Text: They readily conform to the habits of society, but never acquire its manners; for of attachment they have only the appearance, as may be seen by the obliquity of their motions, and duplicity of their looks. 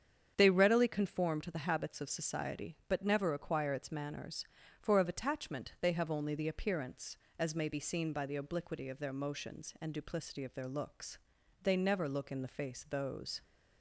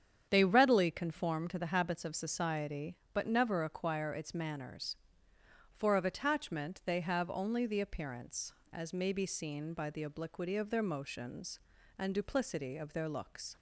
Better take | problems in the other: second | starts louder than the rest; strong; until 1.3 s; 8 dB; strong in the second // goes on to say "They never look in the face those"; strong; from 11.6 s on; 1.8 s long

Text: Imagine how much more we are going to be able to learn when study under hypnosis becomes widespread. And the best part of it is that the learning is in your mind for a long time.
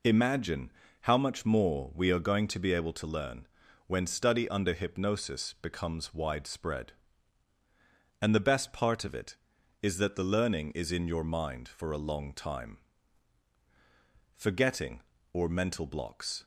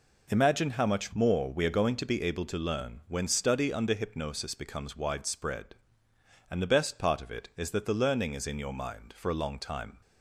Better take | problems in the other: second | pauses between "Imagine" and "how"; slight; at 0.7 s; 0.32 s long // pauses between "learn" and "when"; at 3.4 s; 0.40 s long // goes on to say "Forgetting or mental blocks"; strong; from 14.3 s on; 2.0 s long

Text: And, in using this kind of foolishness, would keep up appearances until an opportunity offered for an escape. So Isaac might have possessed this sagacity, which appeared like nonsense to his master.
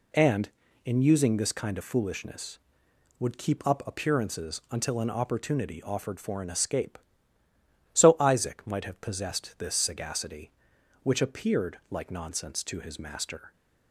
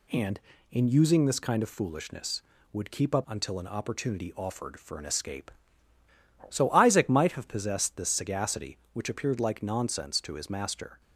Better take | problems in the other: first | skips "appearances"; at 3.2 s

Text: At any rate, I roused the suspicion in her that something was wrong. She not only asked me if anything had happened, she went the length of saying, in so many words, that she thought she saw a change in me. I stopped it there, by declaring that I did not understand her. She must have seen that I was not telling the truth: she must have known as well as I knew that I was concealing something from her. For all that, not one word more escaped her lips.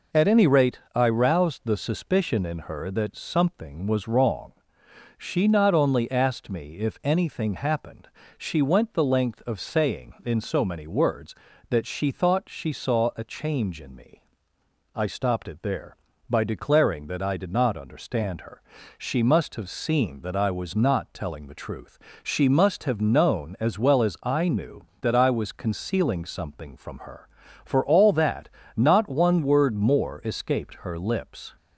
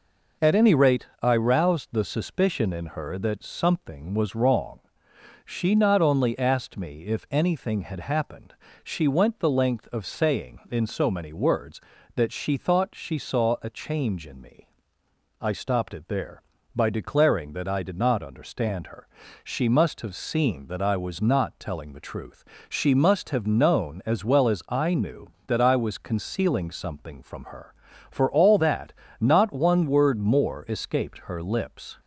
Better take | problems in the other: second | skips "had"; at 7.5 s

